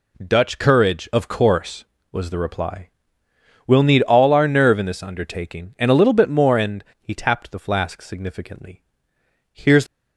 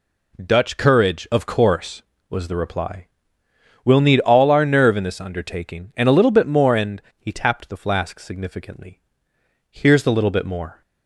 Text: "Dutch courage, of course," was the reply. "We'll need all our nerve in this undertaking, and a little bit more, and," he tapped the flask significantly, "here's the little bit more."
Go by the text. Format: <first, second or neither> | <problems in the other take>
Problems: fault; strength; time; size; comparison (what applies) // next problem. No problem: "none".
second | stops before "the little bit more"; at 9.8 s